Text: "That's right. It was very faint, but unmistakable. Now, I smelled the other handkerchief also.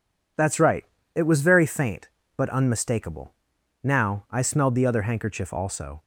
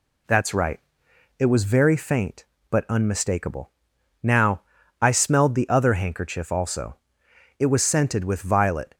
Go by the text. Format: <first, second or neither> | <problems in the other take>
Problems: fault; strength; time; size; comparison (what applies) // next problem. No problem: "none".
first | goes on to say "It was scented with violet"; from 7.5 s on; 1.3 s long